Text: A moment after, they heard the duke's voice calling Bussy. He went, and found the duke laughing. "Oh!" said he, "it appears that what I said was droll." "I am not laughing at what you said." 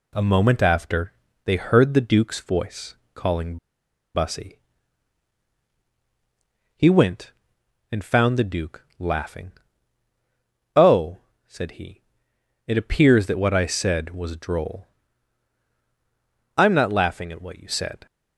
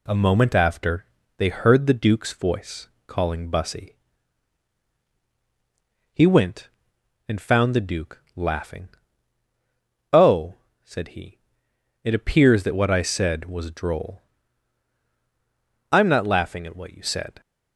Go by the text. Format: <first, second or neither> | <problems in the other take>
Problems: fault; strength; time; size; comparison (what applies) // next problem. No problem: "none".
second | pauses between "voice" and "calling"; slight; at 2.9 s; 0.22 s long; slight in the second // pauses between "calling" and "Bussy"; noticeable; at 3.5 s; 0.58 s long